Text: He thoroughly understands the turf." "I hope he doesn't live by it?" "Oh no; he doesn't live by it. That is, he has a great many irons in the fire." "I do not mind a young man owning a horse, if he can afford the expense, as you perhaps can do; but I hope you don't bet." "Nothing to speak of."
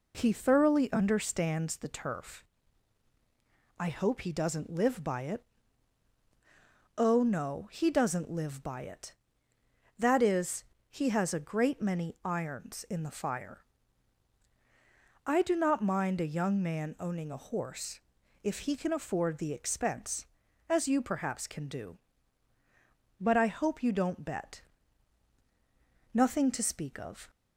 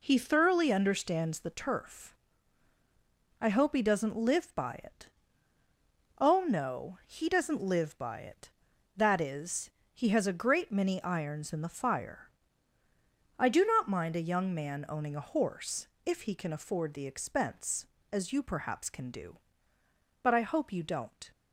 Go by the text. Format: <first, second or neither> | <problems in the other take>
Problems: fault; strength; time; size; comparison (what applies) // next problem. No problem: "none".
first | stops before "bet Nothing to speak of"; at 21.3 s